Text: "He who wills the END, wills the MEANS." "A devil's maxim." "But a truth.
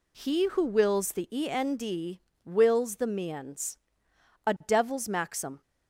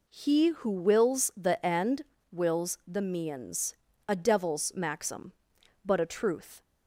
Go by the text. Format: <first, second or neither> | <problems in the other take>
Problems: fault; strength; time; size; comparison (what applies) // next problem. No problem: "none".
second | stops before "But a truth"; at 5.6 s